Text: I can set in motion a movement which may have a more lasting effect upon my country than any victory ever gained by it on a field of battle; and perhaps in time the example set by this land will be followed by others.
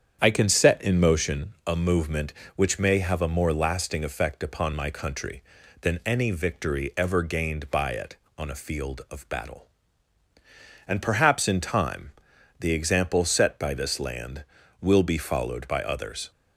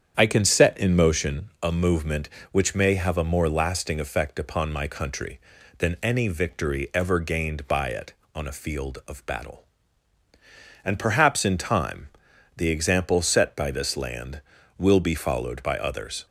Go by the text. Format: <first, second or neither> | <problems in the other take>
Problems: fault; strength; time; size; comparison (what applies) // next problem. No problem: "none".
neither | starts louder than the rest; strong; the same in both // pauses between "time" and "the"; noticeable; the same in both